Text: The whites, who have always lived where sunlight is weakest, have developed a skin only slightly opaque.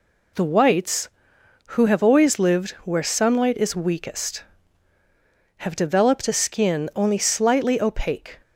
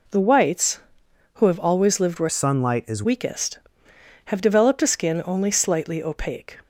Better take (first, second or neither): first